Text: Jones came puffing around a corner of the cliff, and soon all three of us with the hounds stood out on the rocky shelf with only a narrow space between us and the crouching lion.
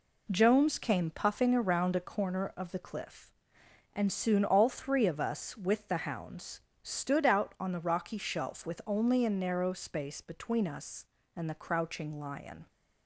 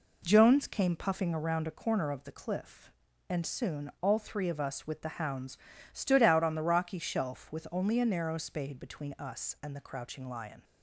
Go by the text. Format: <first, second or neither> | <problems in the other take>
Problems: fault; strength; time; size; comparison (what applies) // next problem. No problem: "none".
first | pauses between "hounds" and "stood"; slight; at 5.5 s; 0.34 s long; slight in the first // says "spade" for "space"; at 8.3 s